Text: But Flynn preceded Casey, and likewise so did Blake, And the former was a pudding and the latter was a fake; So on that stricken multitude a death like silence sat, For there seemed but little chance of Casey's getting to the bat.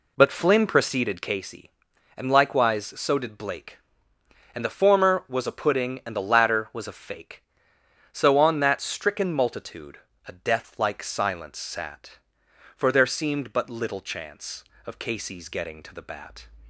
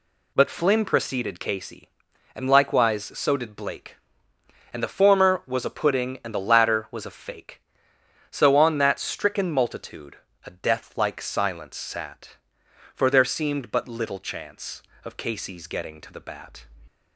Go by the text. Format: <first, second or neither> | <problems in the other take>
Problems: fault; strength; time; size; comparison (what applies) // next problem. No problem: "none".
second | starts louder than the rest; slight; until 1.4 s; 2.5 dB // pauses between "multitude" and "a"; slight; at 9.9 s; 0.28 s long; slight in the second